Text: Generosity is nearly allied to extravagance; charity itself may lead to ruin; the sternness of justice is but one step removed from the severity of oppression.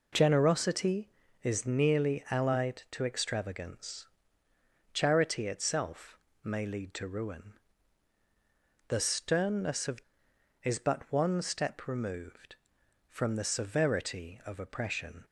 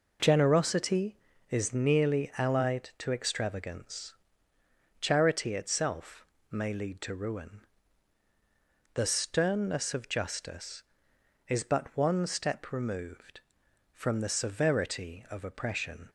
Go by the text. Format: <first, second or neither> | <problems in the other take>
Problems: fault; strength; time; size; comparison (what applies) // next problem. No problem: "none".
second | pauses between "itself" and "may"; slight; at 6.1 s; 0.24 s long; slight in the second // skips "justice"; at 10.3 s